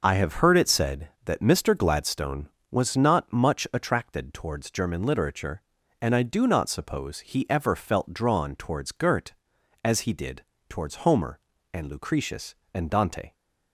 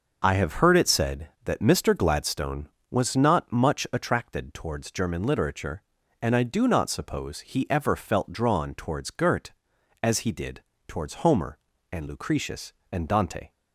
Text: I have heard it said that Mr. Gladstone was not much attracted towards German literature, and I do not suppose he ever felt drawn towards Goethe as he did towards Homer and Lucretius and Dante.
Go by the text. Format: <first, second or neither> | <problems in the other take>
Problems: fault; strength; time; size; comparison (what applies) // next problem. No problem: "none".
neither | pauses between "did" and "towards"; slight; the same in both